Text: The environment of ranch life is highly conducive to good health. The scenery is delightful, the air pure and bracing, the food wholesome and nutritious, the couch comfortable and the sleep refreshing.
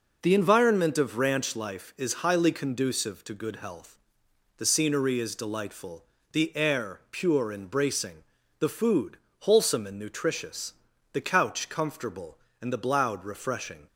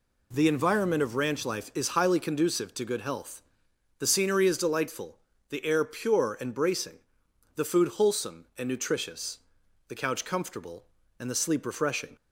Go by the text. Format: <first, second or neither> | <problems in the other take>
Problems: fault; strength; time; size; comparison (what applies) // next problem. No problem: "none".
second | pauses between "food" and "wholesome"; slight; at 9.1 s; 0.22 s long // says "bloud" for "sleep"; at 12.8 s